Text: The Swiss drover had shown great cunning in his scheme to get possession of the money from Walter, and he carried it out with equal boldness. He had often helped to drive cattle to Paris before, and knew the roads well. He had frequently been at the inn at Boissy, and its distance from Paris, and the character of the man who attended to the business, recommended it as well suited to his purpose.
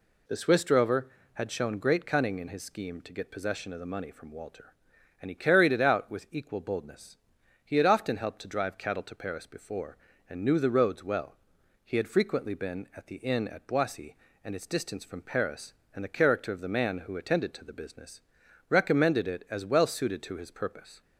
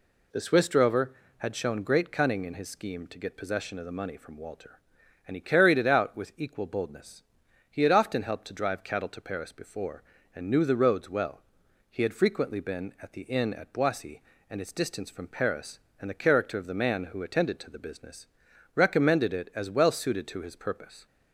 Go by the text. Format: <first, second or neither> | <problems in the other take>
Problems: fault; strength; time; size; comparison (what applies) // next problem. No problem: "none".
neither | none